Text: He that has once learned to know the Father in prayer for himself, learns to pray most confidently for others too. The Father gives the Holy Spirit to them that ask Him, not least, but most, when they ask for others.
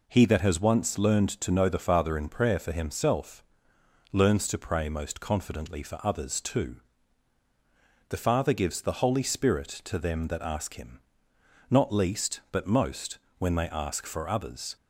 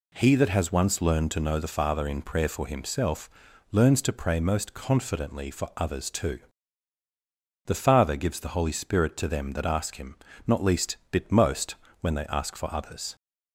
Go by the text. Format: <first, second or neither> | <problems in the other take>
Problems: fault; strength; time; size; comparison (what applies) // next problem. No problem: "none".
first | says "bit" for "but"; at 11.1 s